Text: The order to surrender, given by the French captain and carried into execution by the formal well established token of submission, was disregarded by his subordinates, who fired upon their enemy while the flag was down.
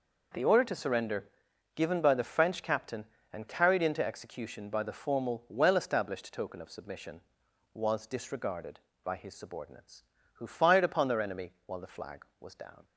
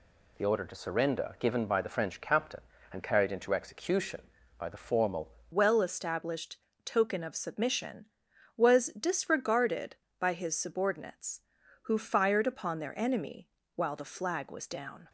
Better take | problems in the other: first | changes voice at "well"; from 5.5 s on; 9.5 s long // pauses between "established" and "token"; slight; at 6.5 s; 0.28 s long // pauses between "enemy" and "while"; slight; at 13.4 s; 0.26 s long

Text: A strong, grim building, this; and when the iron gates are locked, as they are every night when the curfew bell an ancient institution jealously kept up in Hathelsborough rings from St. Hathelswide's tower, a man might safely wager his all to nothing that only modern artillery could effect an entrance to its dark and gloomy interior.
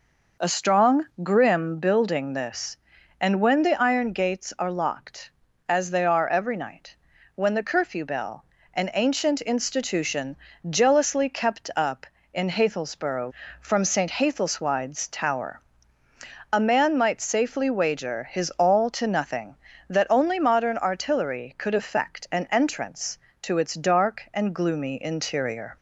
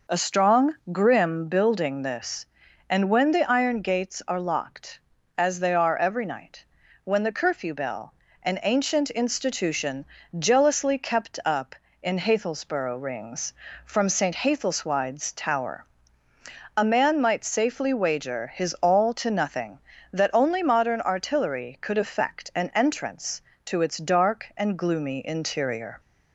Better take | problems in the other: second | pauses between "night" and "when"; at 6.9 s; 0.40 s long; also in the second // pauses between "bell" and "an"; slight; at 8.4 s; 0.28 s long; slight in the second // pauses between "institution" and "jealously"; slight; at 10.3 s; 0.34 s long; slight in the second // skips "rings"; at 13.4 s

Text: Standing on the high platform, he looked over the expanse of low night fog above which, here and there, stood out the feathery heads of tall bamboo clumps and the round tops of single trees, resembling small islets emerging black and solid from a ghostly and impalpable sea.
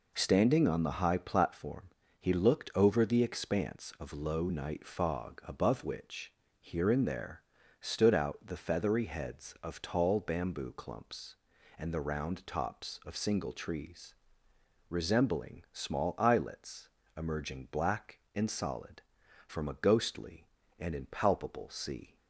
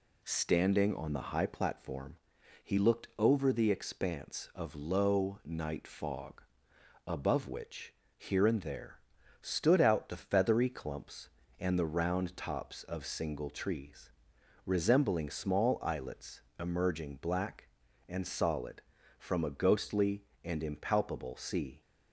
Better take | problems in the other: first | pauses between "fog" and "above"; noticeable; at 6.4 s; 0.64 s long // skips "heads of tall bamboo"; at 10.6 s // pauses between "islets" and "emerging"; slight; at 16.4 s; 0.18 s long; slight in the first

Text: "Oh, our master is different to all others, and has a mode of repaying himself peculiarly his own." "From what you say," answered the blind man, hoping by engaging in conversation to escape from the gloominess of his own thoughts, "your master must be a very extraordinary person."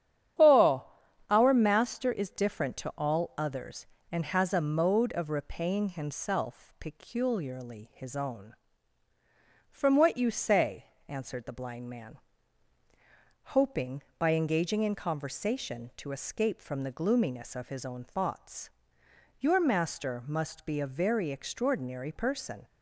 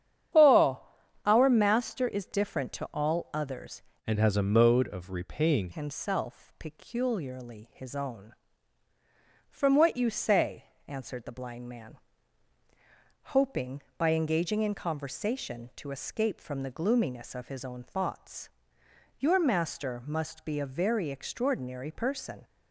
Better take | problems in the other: first | starts louder than the rest; strong; until 1.8 s; 9.5 dB; strong in the first // changes voice from "and" to "repaying"; from 4.0 to 5.7 s; 1.7 s long

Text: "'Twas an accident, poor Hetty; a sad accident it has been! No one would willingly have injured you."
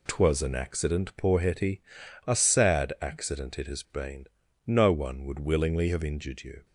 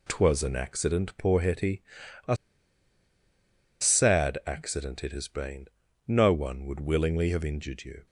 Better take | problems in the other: first | pauses between "a" and "sad"; strong; at 2.3 s; 1.4 s long

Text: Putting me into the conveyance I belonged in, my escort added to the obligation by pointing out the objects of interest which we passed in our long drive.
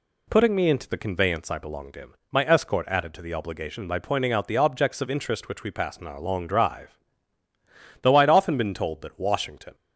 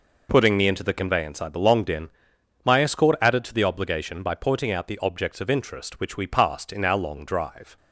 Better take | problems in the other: second | goes on to say "Though I'd often been told that Washington"; strong; from 8.0 s on; 1.7 s long

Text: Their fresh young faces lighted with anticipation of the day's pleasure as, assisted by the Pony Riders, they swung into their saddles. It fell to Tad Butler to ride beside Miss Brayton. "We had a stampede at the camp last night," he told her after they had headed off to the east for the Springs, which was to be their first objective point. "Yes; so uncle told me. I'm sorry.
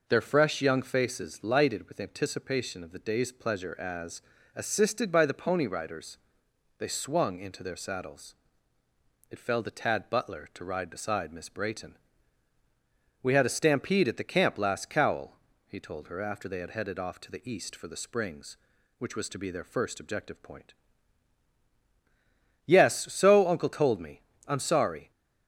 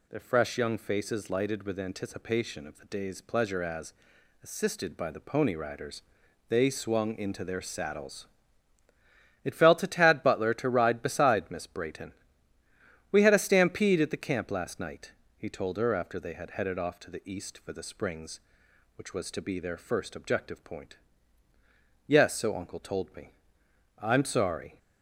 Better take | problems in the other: second | says "cowl" for "night"; at 14.8 s

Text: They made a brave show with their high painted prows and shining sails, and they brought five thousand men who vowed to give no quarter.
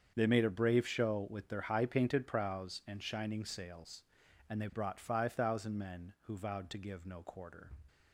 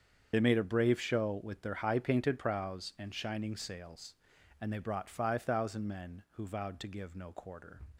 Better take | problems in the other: first | loses the start of "They"; at 0.3 s; 50 ms // starts louder than the rest; strong; until 1.3 s; 7.5 dB; strong in the first

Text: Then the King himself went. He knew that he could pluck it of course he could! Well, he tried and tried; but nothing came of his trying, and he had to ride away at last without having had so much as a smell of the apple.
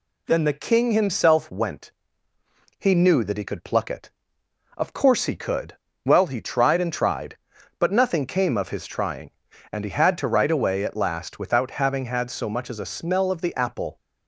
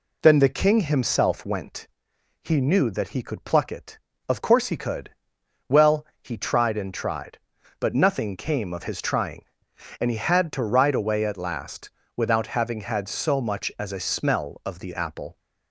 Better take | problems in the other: first | starts louder than the rest; slight; until 1.7 s; 2.5 dB // pauses between "last" and "without"; slight; at 11.9 s; 0.26 s long

